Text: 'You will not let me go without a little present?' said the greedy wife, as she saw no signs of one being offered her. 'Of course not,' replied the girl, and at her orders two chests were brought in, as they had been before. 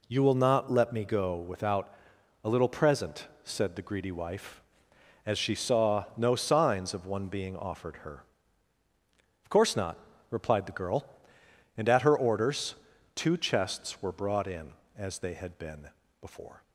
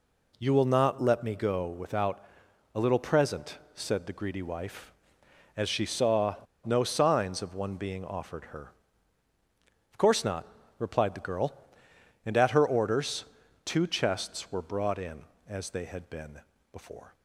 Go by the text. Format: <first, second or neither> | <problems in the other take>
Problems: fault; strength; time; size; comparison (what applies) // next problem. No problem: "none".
first | pauses between "without" and "a"; noticeable; at 2.2 s; 0.50 s long; noticeable in the first // pauses between "saw" and "no"; slight; at 6.3 s; 0.29 s long // pauses between "orders" and "two"; at 13.2 s; 0.40 s long; also in the first // pauses between "been" and "before"; slight; at 16.3 s; 0.32 s long; slight in the first